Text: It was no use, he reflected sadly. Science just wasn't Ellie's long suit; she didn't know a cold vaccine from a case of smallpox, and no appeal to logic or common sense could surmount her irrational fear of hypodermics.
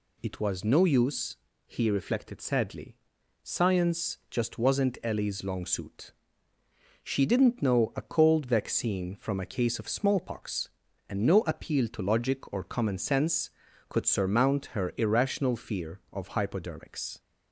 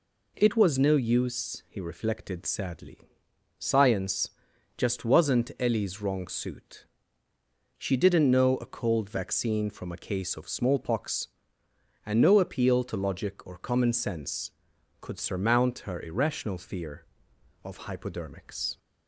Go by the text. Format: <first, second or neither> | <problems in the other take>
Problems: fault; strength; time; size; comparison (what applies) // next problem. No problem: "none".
first | pauses between "Science" and "just"; noticeable; at 4.2 s; 0.46 s long // says "wrong" for "long"; at 6.0 s